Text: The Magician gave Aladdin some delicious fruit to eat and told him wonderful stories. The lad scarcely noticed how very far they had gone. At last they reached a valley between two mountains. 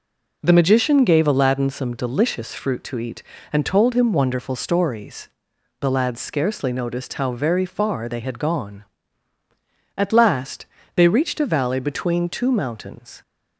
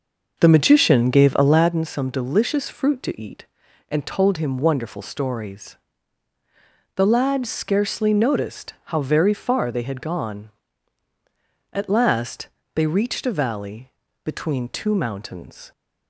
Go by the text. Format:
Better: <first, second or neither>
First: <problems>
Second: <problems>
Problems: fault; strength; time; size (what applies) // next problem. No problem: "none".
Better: first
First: pauses between "last" and "they"; slight; at 10.6 s; 0.30 s long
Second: starts louder than the rest; noticeable; until 1.7 s; 6 dB // pauses between "last" and "they"; slight; at 12.4 s; 0.28 s long // pauses between "valley" and "between"; slight; at 13.8 s; 0.34 s long